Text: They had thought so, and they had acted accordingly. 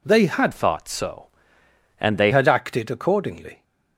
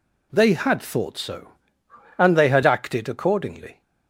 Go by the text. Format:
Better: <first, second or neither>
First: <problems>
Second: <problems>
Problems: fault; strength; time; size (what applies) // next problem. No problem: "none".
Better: second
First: changes voice from "thought" to "they"; from 0.5 to 2.3 s; 1.8 s long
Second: none